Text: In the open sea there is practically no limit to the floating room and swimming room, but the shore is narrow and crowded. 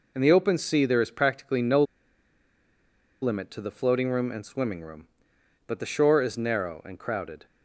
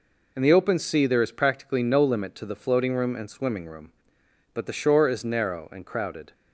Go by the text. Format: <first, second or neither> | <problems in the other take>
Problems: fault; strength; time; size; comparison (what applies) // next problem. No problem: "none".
second | pauses between "no" and "limit"; strong; at 1.8 s; 1.3 s long